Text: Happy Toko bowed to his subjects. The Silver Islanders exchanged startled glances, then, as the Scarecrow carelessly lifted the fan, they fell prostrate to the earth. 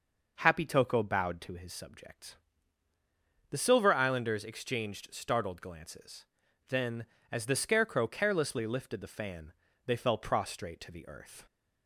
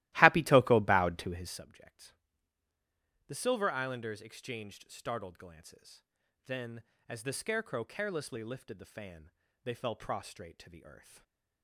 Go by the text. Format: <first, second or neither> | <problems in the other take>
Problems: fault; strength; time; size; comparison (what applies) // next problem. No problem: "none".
first | starts louder than the rest; strong; until 1.7 s; 16.5 dB // stays silent after the last word; slight; from 10.9 s on; 0.7 s long